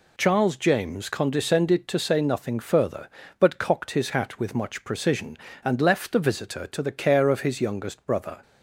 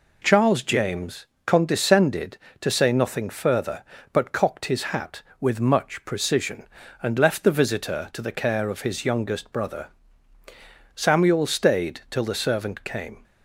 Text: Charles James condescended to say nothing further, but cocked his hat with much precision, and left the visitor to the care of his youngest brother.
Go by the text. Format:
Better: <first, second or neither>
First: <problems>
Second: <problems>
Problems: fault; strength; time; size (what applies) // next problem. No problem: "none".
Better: first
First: none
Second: pauses between "James" and "condescended"; slight; at 1.2 s; 0.18 s long // goes on to say "Samuel stayed till the servant came"; strong; from 10.9 s on; 2.2 s long